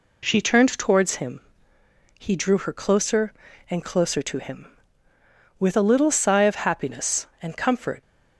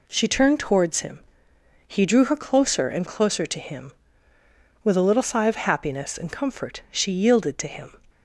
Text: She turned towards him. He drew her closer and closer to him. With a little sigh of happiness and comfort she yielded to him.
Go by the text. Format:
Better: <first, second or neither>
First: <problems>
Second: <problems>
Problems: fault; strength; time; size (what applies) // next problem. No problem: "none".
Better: second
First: stops before "she yielded to him"; at 8.0 s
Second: none